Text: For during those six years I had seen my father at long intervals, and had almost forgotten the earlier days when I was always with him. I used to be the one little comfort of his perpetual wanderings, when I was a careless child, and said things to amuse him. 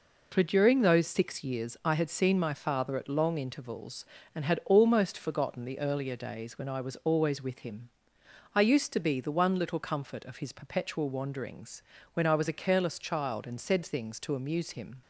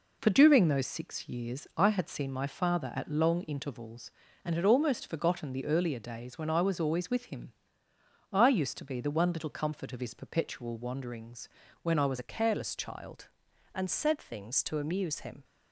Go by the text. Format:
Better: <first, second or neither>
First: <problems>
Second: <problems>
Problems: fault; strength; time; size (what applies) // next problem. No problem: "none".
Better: first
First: none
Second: changes voice at "a"; from 12.1 s on; 3.3 s long